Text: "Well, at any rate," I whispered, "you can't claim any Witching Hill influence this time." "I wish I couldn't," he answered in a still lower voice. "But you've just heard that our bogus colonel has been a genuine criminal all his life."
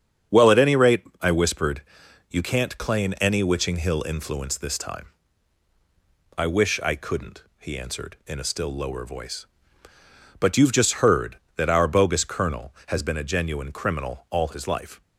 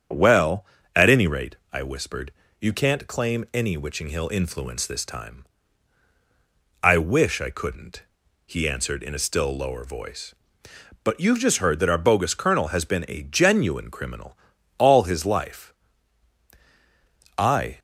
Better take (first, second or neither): first